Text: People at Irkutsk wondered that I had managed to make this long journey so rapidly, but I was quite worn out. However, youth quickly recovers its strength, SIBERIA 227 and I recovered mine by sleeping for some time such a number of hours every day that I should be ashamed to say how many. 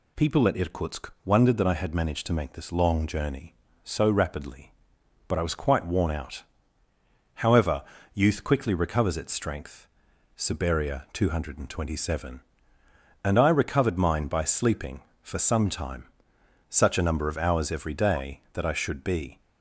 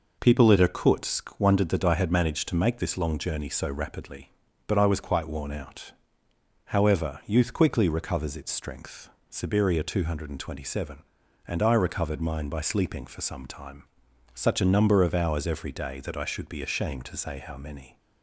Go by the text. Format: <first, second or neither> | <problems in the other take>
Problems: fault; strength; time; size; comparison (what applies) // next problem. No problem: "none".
second | pauses between "time" and "such"; noticeable; at 16.0 s; 0.64 s long; noticeable in the second // stops before "ashamed to say how many"; at 19.3 s